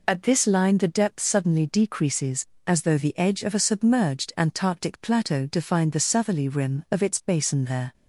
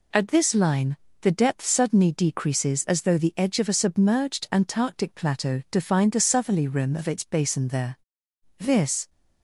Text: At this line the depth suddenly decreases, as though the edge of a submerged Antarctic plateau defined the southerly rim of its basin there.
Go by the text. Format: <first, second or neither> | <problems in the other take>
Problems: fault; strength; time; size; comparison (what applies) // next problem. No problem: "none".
first | pauses between "line" and "the"; slight; at 0.9 s; 0.26 s long // goes on to say "This"; from 8.5 s on; 0.52 s long